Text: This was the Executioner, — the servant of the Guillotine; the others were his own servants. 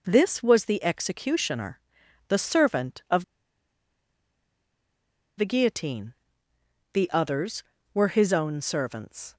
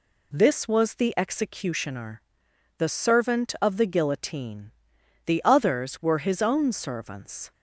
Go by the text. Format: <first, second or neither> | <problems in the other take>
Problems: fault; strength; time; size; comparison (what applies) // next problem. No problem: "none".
second | pauses between "of" and "the"; strong; at 3.2 s; 2.1 s long